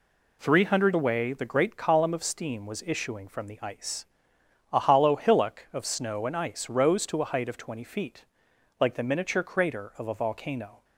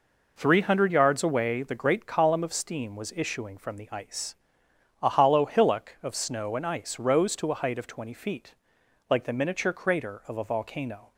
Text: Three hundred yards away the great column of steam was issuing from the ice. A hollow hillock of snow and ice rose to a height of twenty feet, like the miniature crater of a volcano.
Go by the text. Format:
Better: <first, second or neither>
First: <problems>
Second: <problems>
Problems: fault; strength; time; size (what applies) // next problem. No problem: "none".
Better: second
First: skips "yards"; at 0.9 s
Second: none